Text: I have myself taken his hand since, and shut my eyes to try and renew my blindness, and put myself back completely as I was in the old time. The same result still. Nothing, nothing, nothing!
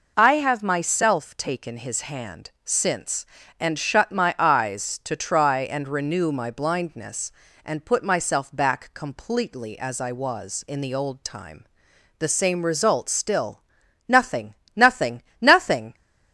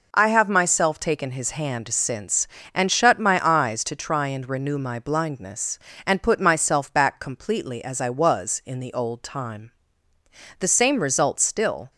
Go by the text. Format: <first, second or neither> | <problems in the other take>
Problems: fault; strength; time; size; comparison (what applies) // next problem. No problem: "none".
first | stops before "Nothing nothing nothing"; at 11.9 s